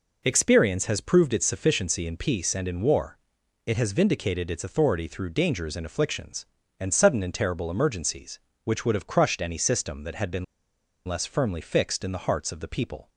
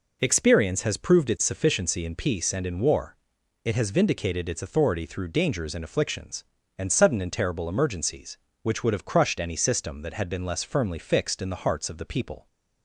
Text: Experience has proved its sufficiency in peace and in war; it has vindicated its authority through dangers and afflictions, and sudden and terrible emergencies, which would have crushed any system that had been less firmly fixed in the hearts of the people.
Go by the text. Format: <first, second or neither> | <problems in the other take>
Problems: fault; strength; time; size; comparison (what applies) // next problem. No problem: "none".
second | pauses between "been" and "less"; noticeable; at 10.4 s; 0.61 s long